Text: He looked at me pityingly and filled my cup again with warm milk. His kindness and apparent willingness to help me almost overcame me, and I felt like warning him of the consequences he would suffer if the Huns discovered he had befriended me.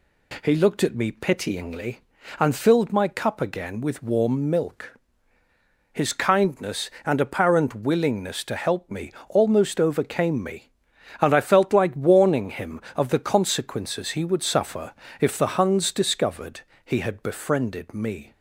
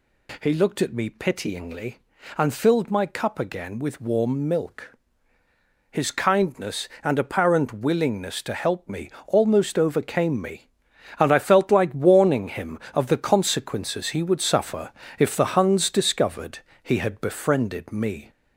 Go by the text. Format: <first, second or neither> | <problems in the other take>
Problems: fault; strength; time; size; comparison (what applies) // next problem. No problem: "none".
first | gets louder; slight; throughout; 3 dB // pauses between "me" and "almost"; slight; at 9.1 s; 0.16 s long; slight in the first // pauses between "suffer" and "if"; slight; at 14.9 s; 0.26 s long; slight in the first // pauses between "discovered" and "he"; slight; at 16.6 s; 0.22 s long; slight in the first